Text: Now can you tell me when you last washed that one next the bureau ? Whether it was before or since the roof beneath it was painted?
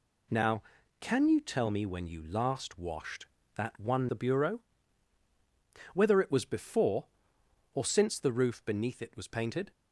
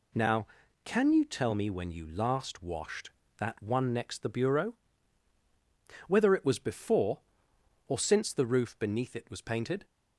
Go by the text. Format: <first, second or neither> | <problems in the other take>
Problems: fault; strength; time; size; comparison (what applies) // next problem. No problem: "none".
second | skips "next"; at 4.0 s